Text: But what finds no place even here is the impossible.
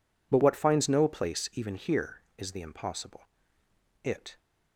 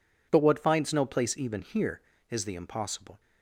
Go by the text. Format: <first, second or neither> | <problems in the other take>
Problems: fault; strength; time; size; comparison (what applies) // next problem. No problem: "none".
second | goes on to say "It"; slight; from 4.0 s on; 0.36 s long